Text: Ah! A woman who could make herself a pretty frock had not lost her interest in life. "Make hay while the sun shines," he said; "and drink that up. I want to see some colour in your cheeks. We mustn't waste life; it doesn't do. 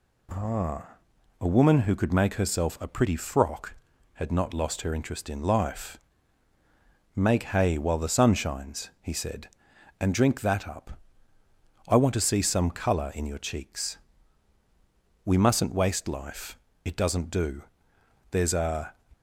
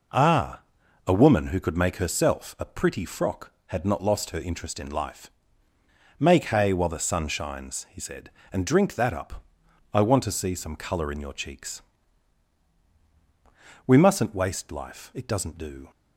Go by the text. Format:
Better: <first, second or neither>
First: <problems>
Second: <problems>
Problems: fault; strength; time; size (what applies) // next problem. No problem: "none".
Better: second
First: goes on to say "There's a"; noticeable; from 18.2 s on; 0.64 s long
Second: none